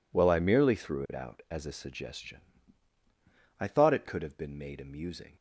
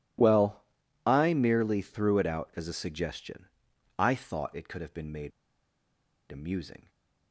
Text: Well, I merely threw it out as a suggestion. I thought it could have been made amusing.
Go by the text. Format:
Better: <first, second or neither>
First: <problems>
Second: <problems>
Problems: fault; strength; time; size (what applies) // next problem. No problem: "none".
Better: first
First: none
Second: pauses between "made" and "amusing"; at 5.3 s; 0.99 s long